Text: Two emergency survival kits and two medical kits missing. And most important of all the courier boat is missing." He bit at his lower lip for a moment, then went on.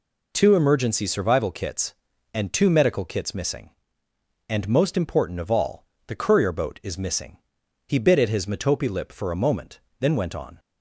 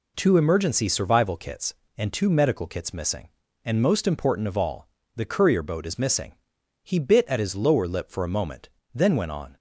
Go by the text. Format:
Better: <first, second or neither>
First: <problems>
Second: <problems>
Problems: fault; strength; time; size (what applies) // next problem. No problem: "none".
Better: second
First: pauses between "all" and "the"; slight; at 5.8 s; 0.22 s long // says "metope" for "lower"; at 8.4 s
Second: pauses between "all" and "the"; slight; at 4.8 s; 0.28 s long